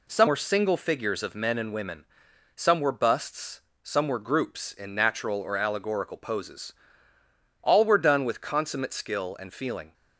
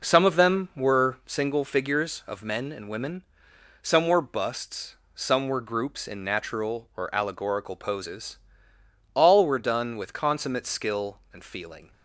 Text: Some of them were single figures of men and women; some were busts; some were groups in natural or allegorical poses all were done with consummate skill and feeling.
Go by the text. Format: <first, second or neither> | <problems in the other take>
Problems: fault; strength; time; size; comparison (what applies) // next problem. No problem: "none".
second | skips "of them"; at 0.2 s // pauses between "poses" and "all"; noticeable; at 6.7 s; 0.88 s long; noticeable in the second